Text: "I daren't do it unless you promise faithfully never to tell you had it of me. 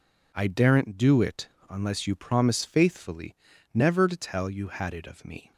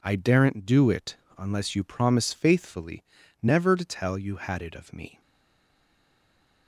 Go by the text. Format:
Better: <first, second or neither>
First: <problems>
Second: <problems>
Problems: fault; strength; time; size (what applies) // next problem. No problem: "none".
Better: first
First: pauses between "it" and "unless"; slight; at 1.4 s; 0.22 s long // pauses between "faithfully" and "never"; at 3.3 s; 0.38 s long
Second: pauses between "it" and "unless"; slight; at 1.1 s; 0.22 s long // pauses between "faithfully" and "never"; at 3.0 s; 0.38 s long // stays silent after the last word; noticeable; from 5.2 s on; 1.4 s long